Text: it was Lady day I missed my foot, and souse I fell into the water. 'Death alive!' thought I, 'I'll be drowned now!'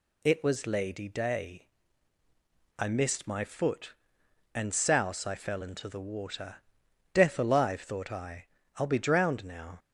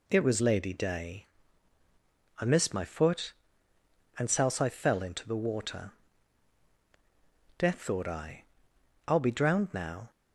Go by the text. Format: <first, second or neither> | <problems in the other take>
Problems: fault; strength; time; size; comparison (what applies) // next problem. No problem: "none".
first | pauses between "day" and "I"; at 1.2 s; 1.1 s long; also in the first // skips "alive"; at 7.8 s